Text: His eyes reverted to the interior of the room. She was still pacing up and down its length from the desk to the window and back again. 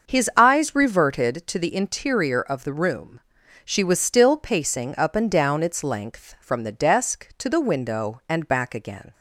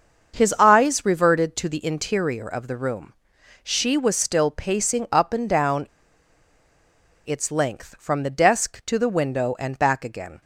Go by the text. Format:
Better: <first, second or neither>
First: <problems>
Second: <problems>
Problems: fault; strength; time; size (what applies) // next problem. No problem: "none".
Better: first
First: starts louder than the rest; noticeable; until 1.1 s; 6 dB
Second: starts louder than the rest; until 1.4 s; 6.5 dB // pauses between "down" and "its"; strong; at 5.8 s; 1.4 s long